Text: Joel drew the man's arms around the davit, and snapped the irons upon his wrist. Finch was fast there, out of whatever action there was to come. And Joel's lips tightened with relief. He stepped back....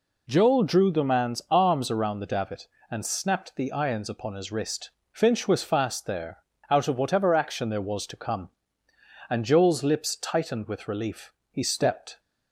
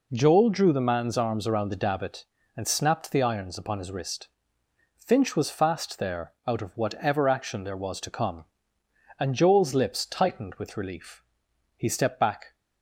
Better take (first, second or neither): second